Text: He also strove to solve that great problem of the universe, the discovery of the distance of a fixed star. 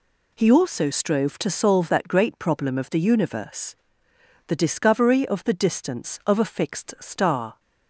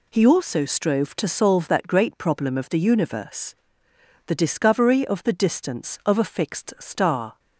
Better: neither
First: none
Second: none

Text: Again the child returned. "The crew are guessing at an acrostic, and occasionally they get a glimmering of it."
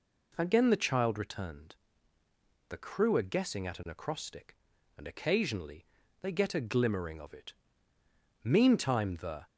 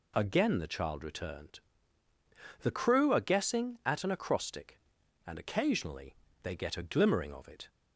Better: second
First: pauses between "occasionally" and "they"; slight; at 5.8 s; 0.34 s long // goes on to say "Meantime the"; noticeable; from 8.4 s on; 1.0 s long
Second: pauses between "occasionally" and "they"; slight; at 6.1 s; 0.28 s long

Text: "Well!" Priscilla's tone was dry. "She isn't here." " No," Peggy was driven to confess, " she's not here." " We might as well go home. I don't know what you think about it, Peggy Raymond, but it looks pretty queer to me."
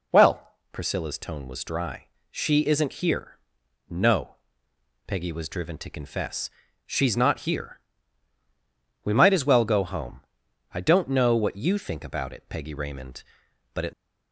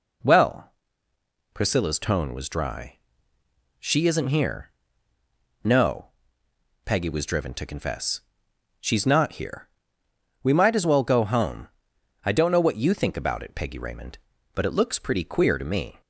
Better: second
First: stops before "looks pretty queer to me"; at 13.9 s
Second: none

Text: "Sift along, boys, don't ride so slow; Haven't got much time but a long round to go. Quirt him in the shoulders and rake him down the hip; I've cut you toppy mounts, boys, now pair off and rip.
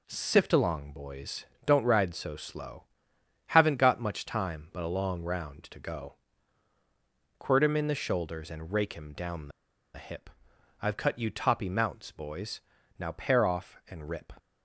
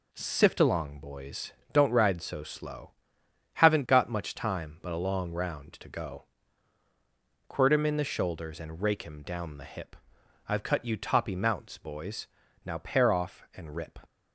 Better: second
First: pauses between "the" and "hip"; noticeable; at 9.5 s; 0.45 s long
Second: none

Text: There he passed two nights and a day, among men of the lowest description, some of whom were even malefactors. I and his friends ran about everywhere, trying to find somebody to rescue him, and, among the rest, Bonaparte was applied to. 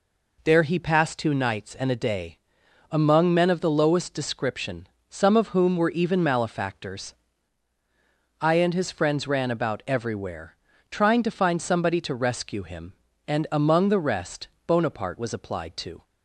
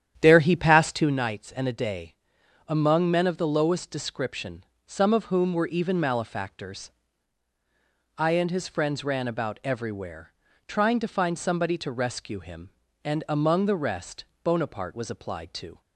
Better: first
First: none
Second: starts louder than the rest; strong; until 1.2 s; 10 dB

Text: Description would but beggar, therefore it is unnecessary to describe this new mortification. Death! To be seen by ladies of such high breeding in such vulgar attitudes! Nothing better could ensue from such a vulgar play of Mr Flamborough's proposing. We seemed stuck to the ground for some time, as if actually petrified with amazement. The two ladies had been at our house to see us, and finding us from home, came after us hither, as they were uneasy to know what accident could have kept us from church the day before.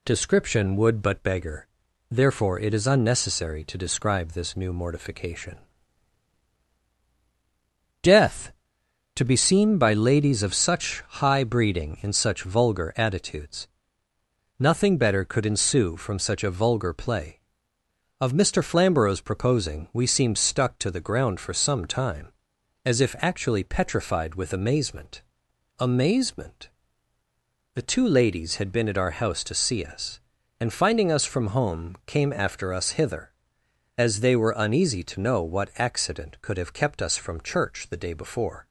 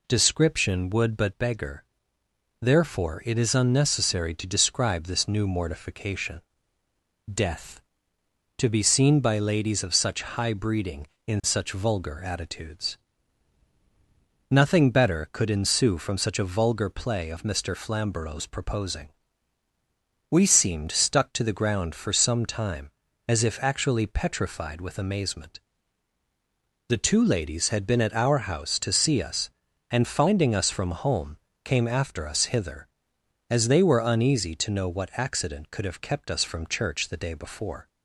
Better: second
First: says "amazement" twice; at 25.7 s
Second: none

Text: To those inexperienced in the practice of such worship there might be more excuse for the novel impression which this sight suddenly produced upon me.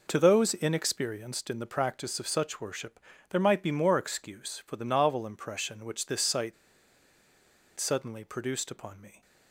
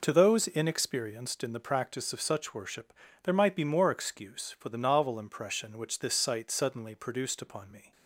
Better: second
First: pauses between "worship" and "there"; slight; at 2.9 s; 0.34 s long // pauses between "sight" and "suddenly"; strong; at 6.5 s; 1.2 s long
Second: pauses between "worship" and "there"; slight; at 2.9 s; 0.34 s long

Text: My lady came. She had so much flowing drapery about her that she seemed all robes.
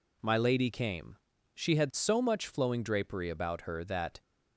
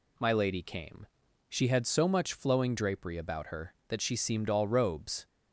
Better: second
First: stops before "she seemed all robes"; at 4.2 s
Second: none

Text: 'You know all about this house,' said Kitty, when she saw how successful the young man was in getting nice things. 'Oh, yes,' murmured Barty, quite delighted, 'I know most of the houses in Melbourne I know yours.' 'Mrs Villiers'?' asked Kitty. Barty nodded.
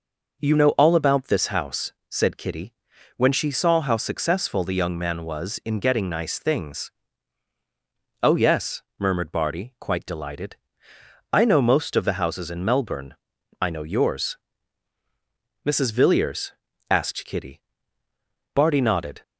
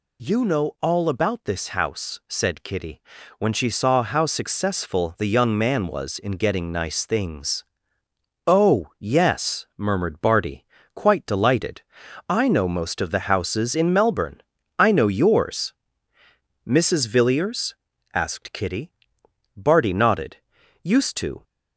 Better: first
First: pauses between "Melbourne" and "I"; noticeable; at 13.1 s; 0.46 s long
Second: pauses between "Melbourne" and "I"; at 14.3 s; 0.40 s long // goes on to say "Used to"; from 20.8 s on; 0.58 s long

